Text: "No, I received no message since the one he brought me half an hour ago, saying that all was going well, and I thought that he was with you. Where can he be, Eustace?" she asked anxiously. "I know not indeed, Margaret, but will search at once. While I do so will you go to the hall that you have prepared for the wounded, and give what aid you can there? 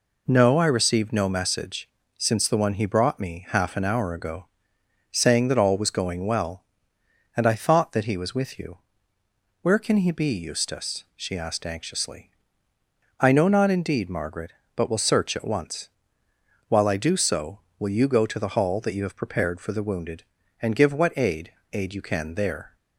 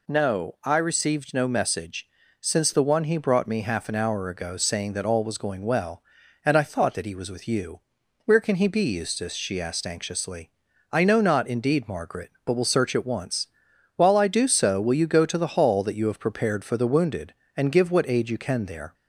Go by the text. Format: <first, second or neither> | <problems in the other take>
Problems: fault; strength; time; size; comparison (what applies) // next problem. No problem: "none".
second | pauses between "message" and "since"; slight; at 1.8 s; 0.30 s long; slight in the second // says "aid" twice; at 21.7 s